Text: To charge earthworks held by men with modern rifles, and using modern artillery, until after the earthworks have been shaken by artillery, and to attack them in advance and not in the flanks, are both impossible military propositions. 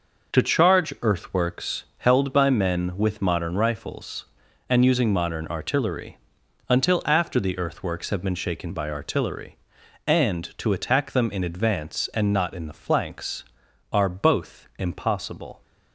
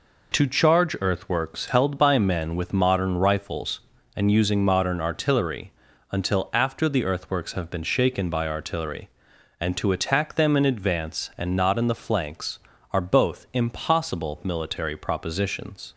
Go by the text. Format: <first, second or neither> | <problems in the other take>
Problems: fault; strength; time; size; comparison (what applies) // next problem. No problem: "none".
second | pauses between "earthworks" and "held"; slight; at 1.8 s; 0.16 s long // stops before "military propositions"; at 15.6 s